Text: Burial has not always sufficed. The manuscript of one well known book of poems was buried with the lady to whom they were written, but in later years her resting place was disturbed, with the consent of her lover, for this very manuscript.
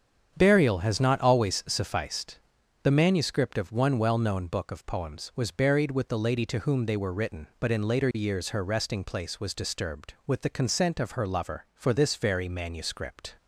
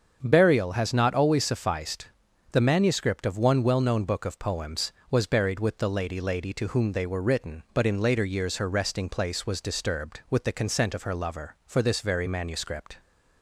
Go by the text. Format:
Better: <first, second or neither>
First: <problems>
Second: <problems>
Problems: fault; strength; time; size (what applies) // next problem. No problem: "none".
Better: first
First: starts louder than the rest; strong; until 1.3 s; 8 dB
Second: starts louder than the rest; until 1.2 s; 7 dB // says "lady" twice; at 6.2 s